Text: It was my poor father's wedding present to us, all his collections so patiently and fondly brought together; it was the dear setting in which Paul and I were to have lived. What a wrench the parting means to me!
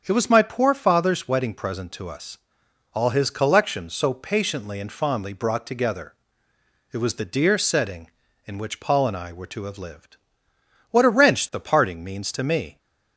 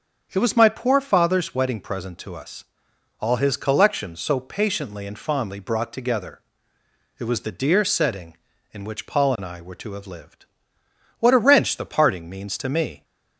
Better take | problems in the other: neither | starts louder than the rest; strong; the same in both

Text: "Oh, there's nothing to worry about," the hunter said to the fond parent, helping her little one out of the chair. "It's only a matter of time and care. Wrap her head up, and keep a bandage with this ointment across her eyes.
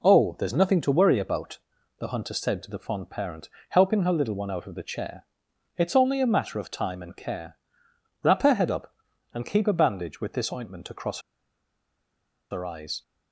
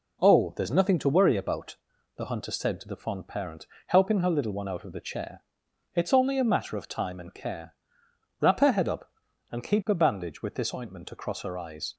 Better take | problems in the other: second | pauses between "across" and "her"; strong; at 11.1 s; 1.3 s long

